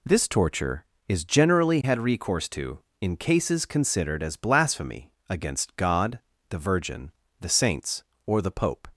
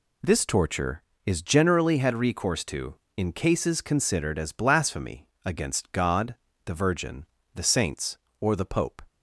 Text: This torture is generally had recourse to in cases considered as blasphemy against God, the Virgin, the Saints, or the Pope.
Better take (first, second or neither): neither